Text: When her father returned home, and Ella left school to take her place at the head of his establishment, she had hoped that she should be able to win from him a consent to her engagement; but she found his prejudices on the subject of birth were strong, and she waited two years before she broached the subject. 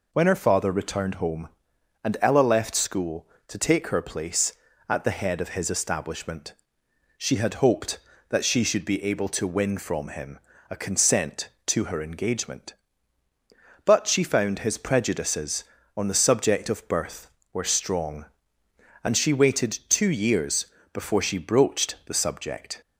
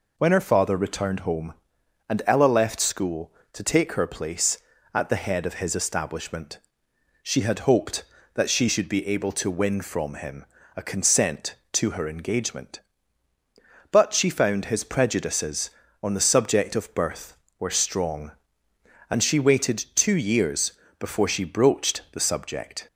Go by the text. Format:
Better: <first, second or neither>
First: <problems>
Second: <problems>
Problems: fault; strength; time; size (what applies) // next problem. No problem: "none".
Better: neither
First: pauses between "him" and "a"; slight; at 10.3 s; 0.32 s long // pauses between "years" and "before"; slight; at 20.6 s; 0.30 s long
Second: pauses between "him" and "a"; slight; at 10.4 s; 0.32 s long // pauses between "years" and "before"; slight; at 20.7 s; 0.30 s long